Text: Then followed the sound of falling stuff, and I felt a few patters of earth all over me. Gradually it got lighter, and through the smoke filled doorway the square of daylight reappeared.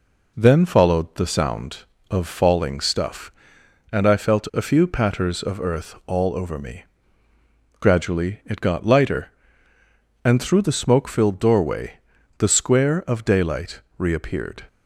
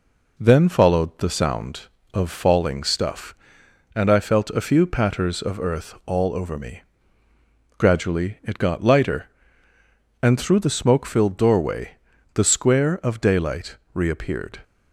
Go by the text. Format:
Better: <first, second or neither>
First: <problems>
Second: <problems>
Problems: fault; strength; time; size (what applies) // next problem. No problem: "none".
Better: neither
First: pauses between "doorway" and "the"; at 11.9 s; 0.44 s long // pauses between "daylight" and "reappeared"; slight; at 13.8 s; 0.16 s long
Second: pauses between "doorway" and "the"; at 11.9 s; 0.42 s long // pauses between "daylight" and "reappeared"; slight; at 13.7 s; 0.16 s long